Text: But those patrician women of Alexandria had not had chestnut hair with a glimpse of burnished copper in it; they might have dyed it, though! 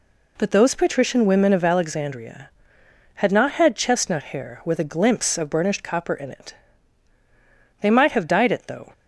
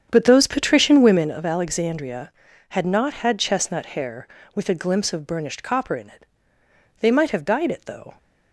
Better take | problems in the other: first | starts louder than the rest; strong; until 1.2 s; 8 dB

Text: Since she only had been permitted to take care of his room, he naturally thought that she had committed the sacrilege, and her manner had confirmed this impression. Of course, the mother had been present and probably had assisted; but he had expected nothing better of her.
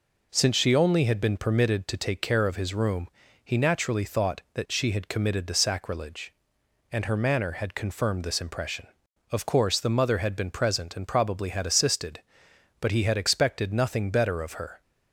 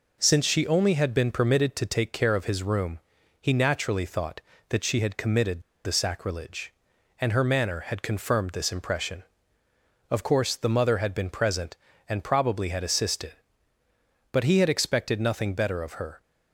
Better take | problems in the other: first | pauses between "committed" and "the"; slight; at 5.6 s; 0.23 s long

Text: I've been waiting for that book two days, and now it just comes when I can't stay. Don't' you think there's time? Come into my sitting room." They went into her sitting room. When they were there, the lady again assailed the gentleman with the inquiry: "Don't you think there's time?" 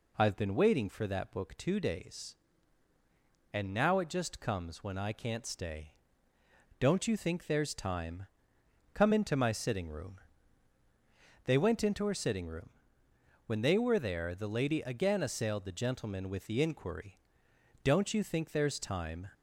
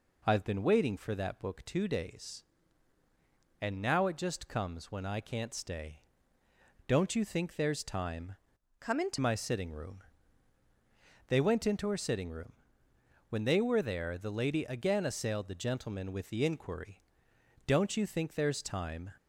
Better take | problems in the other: first | changes voice from "Come" to "into"; from 8.7 to 9.1 s; 0.4 s long

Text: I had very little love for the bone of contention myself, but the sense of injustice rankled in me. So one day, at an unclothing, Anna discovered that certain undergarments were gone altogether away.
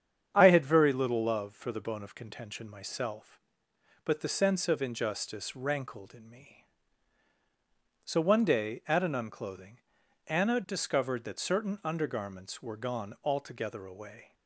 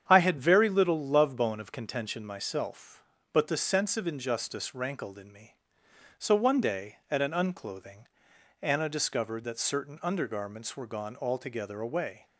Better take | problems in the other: first | starts louder than the rest; strong; until 1.0 s; 8.5 dB; strong in the first // skips "for the"; at 1.3 s

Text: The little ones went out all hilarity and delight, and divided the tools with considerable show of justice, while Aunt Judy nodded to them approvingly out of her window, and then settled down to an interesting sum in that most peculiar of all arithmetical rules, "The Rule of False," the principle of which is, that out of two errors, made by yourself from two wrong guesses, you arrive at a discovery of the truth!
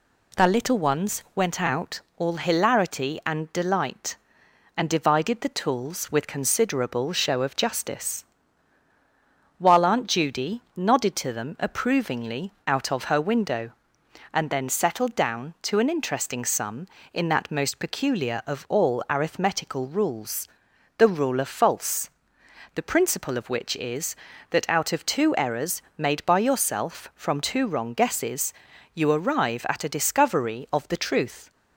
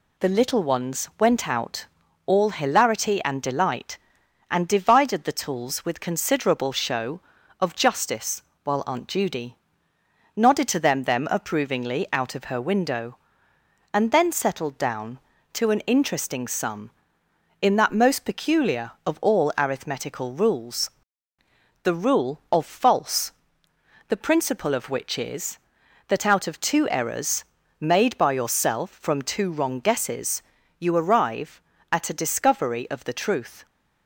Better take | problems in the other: first | pauses between "out" and "all"; at 1.8 s; 0.40 s long; slight in the first // pauses between "Judy" and "nodded"; noticeable; at 9.5 s; 0.80 s long // says "them" twice; at 11.0 s

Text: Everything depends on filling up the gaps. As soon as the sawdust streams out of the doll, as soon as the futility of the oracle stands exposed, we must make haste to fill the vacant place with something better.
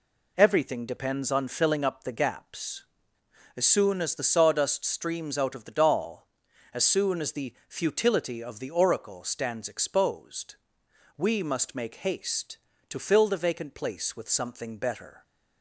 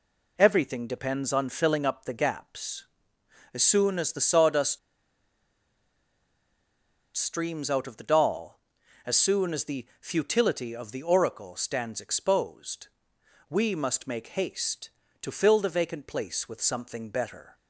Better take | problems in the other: first | pauses between "sawdust" and "streams"; strong; at 4.7 s; 2.3 s long

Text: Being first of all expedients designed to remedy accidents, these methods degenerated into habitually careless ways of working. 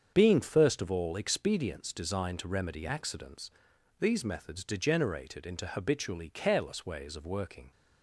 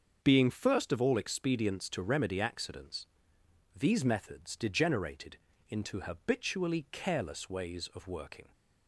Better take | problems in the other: first | starts louder than the rest; until 1.2 s; 6.5 dB; strong in the first // skips "designed"; at 1.9 s // pauses between "degenerated" and "into"; slight; at 5.3 s; 0.32 s long

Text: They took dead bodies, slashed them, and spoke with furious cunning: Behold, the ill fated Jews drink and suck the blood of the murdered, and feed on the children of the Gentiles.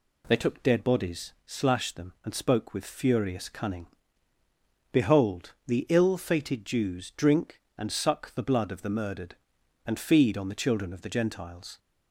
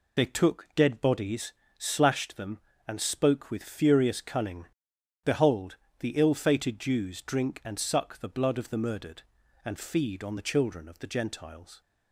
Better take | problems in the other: first | loses the start of "They"; at 0.1 s; 45 ms

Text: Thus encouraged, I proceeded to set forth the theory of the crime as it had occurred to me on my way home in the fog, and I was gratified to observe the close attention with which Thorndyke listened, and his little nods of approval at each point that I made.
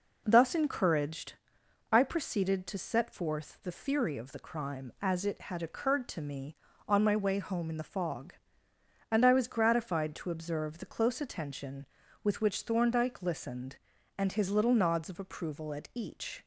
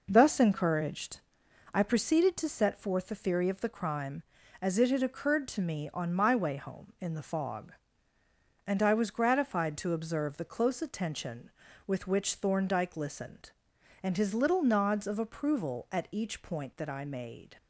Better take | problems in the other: second | stops before "point that I made"; at 16.4 s

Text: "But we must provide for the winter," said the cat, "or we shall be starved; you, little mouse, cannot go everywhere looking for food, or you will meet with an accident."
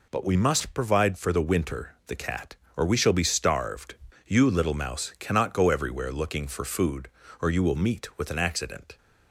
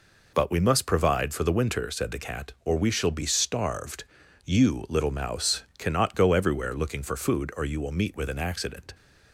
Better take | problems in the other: second | skips "said"; at 2.0 s

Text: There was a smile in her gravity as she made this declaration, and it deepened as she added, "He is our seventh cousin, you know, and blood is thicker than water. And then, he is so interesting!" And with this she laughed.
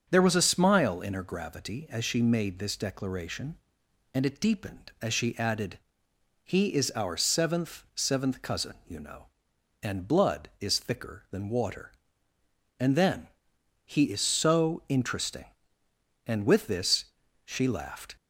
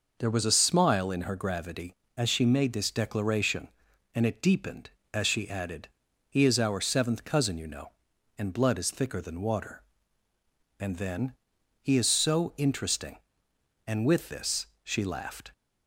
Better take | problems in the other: second | starts louder than the rest; until 1.1 s; 7 dB // says "seventh" twice; at 7.9 s // pauses between "this" and "she"; at 17.0 s; 0.38 s long; slight in the second

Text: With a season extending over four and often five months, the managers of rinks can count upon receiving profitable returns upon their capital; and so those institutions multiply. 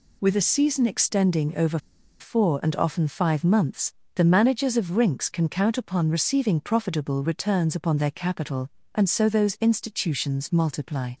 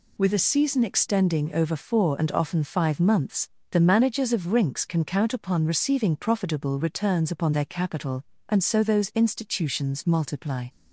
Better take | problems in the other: second | pauses between "over" and "four"; at 1.7 s; 0.42 s long

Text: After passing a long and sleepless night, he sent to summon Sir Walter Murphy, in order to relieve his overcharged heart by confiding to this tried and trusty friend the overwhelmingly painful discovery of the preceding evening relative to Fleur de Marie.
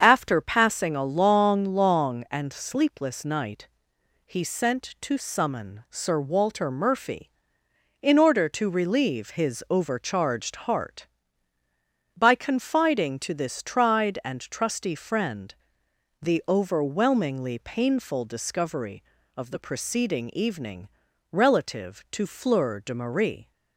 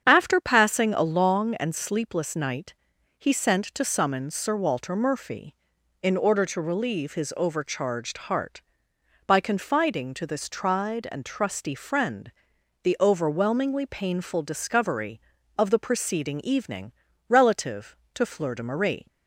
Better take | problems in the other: second | starts louder than the rest; strong; until 1.0 s; 7.5 dB; strong in the second // says "long" twice; at 1.6 s // pauses between "friend" and "the"; noticeable; at 15.5 s; 0.66 s long; noticeable in the second // pauses between "evening" and "relative"; at 20.8 s; 0.44 s long; also in the second

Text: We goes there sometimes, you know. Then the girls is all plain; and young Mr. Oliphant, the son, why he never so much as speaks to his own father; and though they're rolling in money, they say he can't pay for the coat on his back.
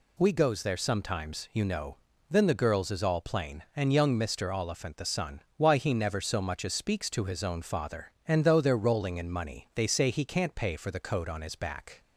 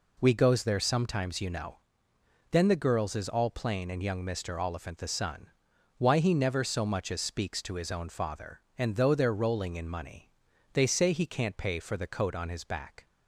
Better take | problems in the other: neither | none

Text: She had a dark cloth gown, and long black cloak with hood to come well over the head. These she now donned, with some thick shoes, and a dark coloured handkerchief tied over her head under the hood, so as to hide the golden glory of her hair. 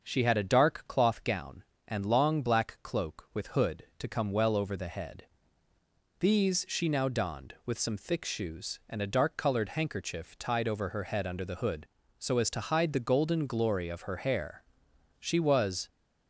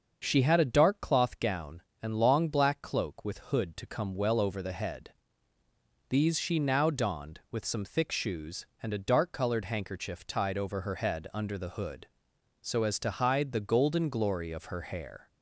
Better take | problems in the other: second | starts louder than the rest; until 1.0 s; 6 dB; also in the second // goes on to say "She was"; noticeable; from 15.2 s on; 0.68 s long

